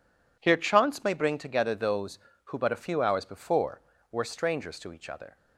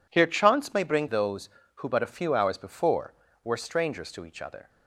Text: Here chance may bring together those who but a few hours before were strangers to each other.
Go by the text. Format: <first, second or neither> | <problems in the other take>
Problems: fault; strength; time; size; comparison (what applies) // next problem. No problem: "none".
first | skips "together"; at 1.0 s